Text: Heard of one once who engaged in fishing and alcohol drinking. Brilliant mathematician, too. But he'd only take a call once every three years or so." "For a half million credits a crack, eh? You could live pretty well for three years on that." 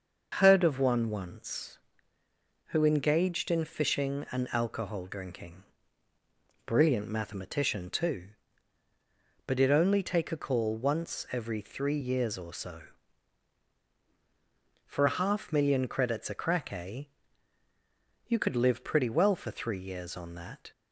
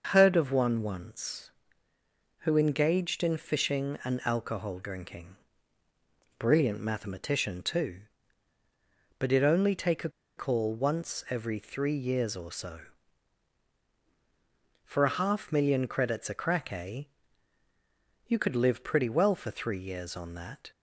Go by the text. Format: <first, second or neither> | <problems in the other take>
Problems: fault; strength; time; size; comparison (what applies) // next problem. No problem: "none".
first | starts louder than the rest; noticeable; until 1.1 s; 6 dB; noticeable in the first // pauses between "a" and "call"; slight; at 10.0 s; 0.27 s long